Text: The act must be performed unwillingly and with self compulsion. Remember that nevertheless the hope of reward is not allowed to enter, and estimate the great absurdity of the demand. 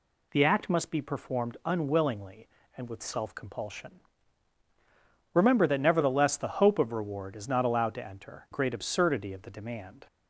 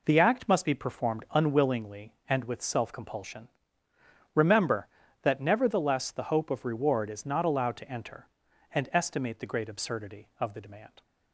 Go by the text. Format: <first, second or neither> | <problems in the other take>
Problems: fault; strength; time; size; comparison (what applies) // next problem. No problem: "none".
second | skips "and estimate the"; at 8.4 s